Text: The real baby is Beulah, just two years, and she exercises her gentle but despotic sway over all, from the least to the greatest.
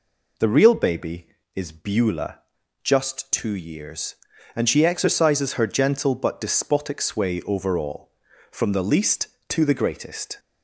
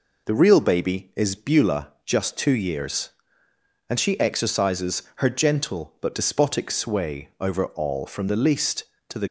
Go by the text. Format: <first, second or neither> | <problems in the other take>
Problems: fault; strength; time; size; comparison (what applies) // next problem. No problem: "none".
first | stops before "greatest"; at 9.2 s